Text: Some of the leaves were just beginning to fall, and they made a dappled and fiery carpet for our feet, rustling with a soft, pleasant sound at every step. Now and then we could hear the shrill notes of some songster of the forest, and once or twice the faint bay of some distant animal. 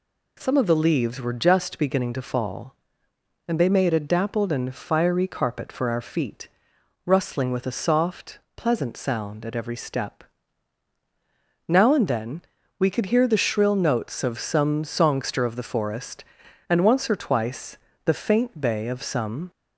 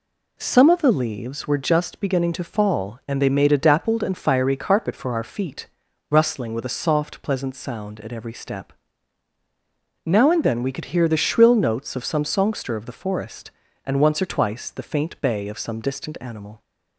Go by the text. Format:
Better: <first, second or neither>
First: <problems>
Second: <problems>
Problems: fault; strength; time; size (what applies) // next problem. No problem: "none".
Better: second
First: pauses between "then" and "we"; slight; at 12.4 s; 0.36 s long // pauses between "twice" and "the"; slight; at 17.7 s; 0.28 s long // stops before "distant animal"; at 19.4 s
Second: none